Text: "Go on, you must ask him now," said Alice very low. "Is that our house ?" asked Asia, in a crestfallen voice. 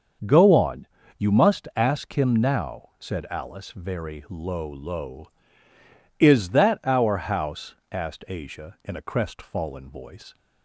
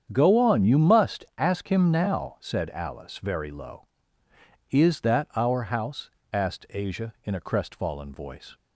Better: second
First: starts louder than the rest; until 1.5 s; 6.5 dB // says "low" twice; at 4.6 s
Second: starts louder than the rest; strong; until 1.1 s; 8 dB

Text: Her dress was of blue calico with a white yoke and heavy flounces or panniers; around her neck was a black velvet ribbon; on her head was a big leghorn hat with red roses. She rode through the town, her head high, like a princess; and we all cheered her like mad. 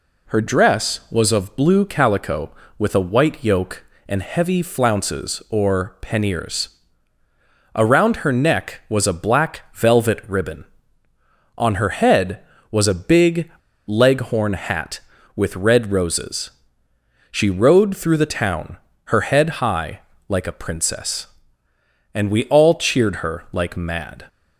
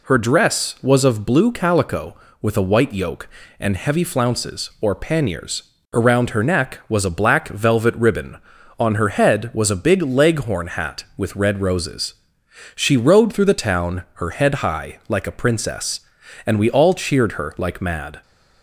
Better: second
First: pauses between "big" and "leghorn"; at 13.4 s; 0.38 s long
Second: none

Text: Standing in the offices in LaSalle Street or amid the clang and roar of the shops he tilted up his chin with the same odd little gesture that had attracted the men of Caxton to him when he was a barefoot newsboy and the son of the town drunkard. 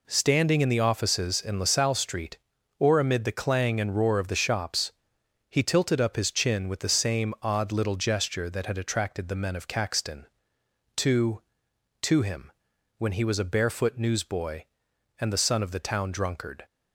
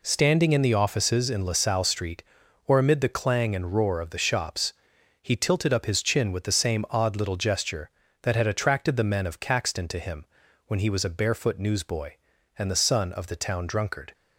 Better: second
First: pauses between "shops" and "he"; noticeable; at 4.9 s; 0.58 s long // says "to" twice; at 12.0 s // pauses between "him" and "when"; noticeable; at 12.5 s; 0.48 s long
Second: pauses between "shops" and "he"; noticeable; at 4.7 s; 0.52 s long // pauses between "him" and "when"; at 10.2 s; 0.42 s long

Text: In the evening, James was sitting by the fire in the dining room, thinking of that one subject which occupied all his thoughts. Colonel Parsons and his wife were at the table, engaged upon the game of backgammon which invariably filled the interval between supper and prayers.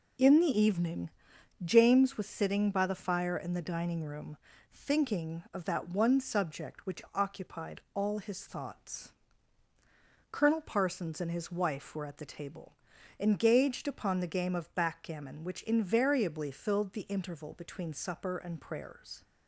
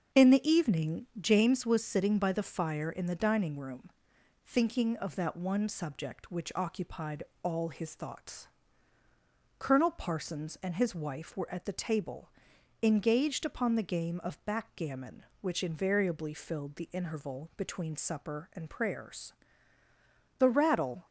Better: first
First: none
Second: starts louder than the rest; until 1.2 s; 6.5 dB // pauses between "occupied" and "all"; slight; at 7.2 s; 0.20 s long // goes on to say "The rattle"; noticeable; from 20.3 s on; 0.66 s long

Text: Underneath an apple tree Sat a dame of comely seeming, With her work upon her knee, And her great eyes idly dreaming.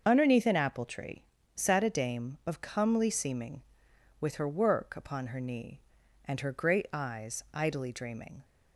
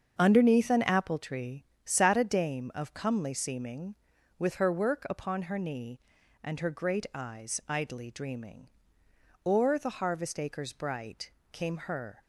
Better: first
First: starts louder than the rest; until 1.0 s; 6.5 dB // pauses between "tree" and "Sat"; slight; at 1.2 s; 0.30 s long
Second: starts louder than the rest; until 1.2 s; 7 dB // pauses between "tree" and "Sat"; slight; at 1.6 s; 0.22 s long // goes on to say "O'er the harvest acres bright Came her"; strong; from 9.4 s on; 2.7 s long

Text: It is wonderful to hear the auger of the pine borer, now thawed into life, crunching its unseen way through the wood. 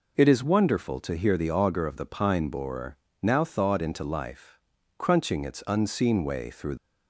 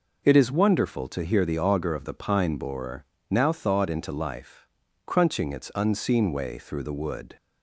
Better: second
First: stops before "the wood"; at 6.7 s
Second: none

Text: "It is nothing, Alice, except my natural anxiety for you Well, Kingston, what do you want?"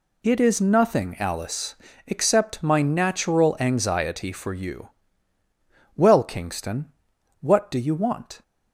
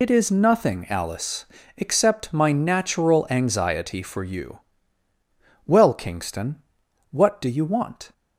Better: first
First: pauses between "you" and "Well"; at 4.8 s; 1.0 s long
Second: loses the start of "It"; at 0.0 s; 65 ms // pauses between "you" and "Well"; at 4.5 s; 1.0 s long

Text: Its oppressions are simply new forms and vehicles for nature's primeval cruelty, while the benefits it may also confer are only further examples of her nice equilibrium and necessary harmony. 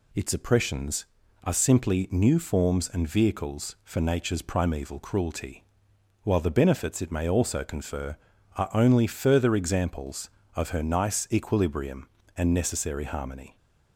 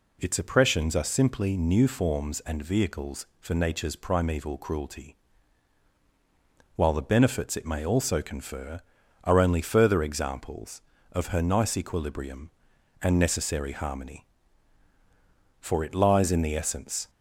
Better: first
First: none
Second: goes on to say "For it lies in the essence"; from 15.5 s on; 1.5 s long

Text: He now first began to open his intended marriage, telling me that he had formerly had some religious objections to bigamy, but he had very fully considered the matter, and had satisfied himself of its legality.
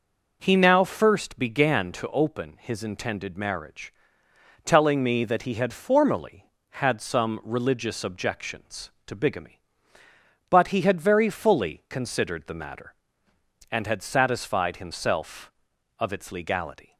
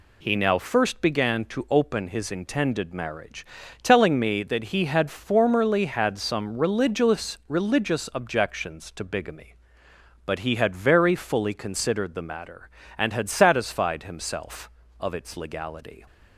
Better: first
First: none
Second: says "religious" twice; at 7.4 s

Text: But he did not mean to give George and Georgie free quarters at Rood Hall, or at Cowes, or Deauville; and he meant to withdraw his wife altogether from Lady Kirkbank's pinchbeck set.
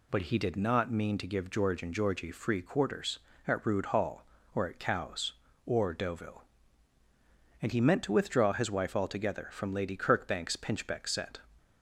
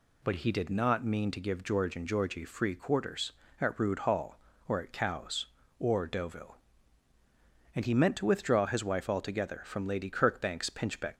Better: first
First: none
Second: stops before "set"; at 11.1 s

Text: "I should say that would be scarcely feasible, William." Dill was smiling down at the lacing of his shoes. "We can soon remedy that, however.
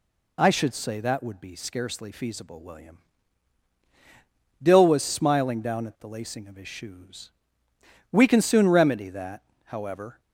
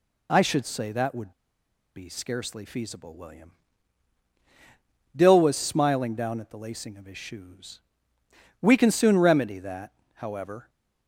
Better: first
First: none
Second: pauses between "would" and "be"; noticeable; at 1.3 s; 0.62 s long

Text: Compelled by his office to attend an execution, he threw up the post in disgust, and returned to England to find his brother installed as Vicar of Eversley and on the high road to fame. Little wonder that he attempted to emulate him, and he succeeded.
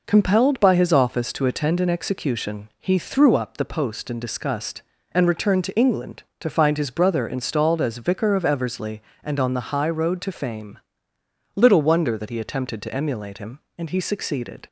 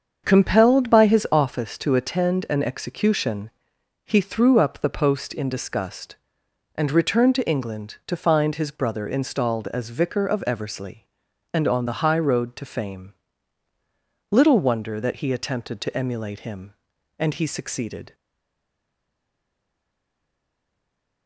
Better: first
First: none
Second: starts louder than the rest; strong; until 1.2 s; 7 dB // stays silent after the last word; strong; from 18.1 s on; 3.1 s long

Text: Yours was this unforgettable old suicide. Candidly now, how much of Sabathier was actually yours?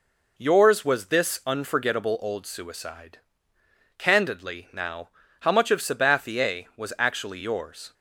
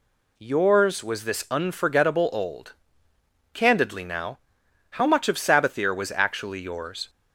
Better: first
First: none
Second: skips "suicide"; at 3.1 s

